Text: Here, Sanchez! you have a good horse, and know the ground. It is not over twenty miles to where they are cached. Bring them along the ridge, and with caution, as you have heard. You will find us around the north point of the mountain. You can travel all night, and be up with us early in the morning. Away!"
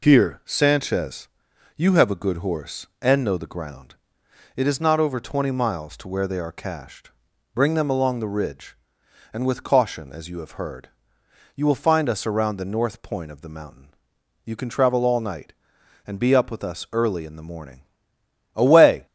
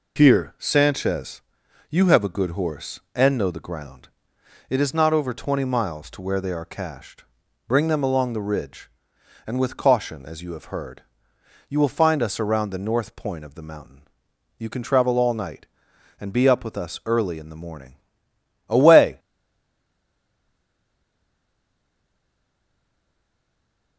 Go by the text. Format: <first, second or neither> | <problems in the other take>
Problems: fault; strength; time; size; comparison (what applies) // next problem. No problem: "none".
first | stays silent after the last word; strong; from 19.1 s on; 4.8 s long